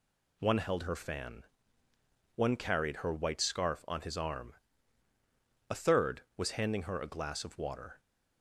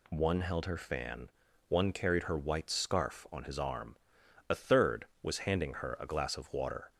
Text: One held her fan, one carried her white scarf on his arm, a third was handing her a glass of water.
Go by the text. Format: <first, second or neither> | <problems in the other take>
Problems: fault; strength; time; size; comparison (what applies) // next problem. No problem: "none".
neither | none